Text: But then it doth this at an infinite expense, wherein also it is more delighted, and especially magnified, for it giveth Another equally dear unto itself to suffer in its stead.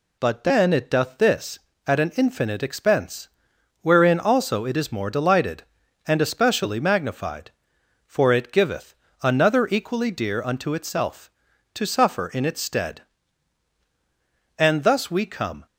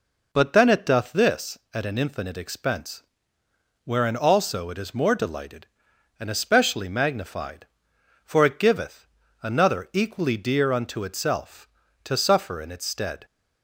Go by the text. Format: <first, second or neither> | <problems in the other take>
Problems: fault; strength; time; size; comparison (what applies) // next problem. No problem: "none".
second | pauses between "giveth" and "Another"; slight; at 8.9 s; 0.28 s long; also in the second // goes on to say "And thus we come"; noticeable; from 14.5 s on; 1.0 s long